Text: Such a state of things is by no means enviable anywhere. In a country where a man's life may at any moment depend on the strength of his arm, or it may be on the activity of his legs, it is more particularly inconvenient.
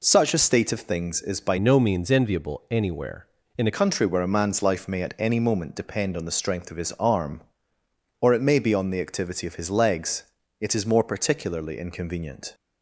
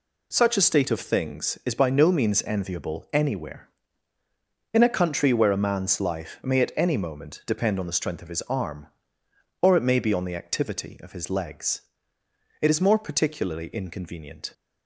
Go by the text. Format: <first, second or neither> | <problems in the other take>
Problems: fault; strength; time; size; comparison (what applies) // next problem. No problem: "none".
second | changes voice from "no" to "a"; from 1.5 to 3.7 s; 2.2 s long